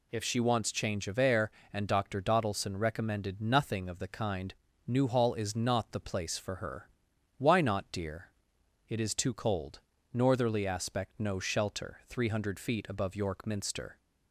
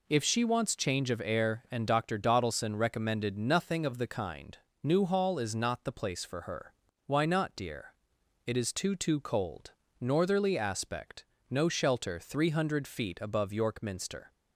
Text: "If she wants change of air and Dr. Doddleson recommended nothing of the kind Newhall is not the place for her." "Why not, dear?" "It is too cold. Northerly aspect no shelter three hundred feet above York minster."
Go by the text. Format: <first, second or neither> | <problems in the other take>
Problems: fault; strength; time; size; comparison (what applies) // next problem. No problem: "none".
first | pauses between "kind" and "Newhall"; slight; at 4.5 s; 0.28 s long; slight in the first // says "too" twice; at 8.9 s // pauses between "aspect" and "no"; slight; at 11.2 s; 0.24 s long